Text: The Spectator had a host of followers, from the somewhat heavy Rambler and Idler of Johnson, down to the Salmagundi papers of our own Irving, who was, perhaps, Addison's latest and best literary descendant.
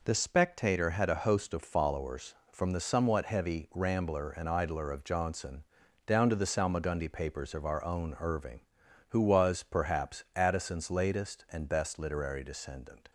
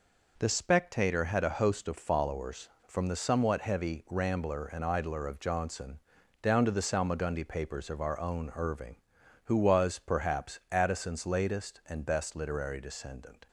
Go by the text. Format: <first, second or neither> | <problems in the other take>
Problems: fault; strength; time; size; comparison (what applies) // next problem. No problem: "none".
neither | none